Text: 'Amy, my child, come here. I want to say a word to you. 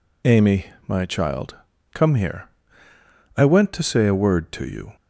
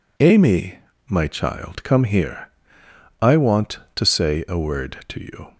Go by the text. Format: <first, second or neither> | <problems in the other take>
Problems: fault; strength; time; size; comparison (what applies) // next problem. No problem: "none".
second | says "went" for "want"; at 3.4 s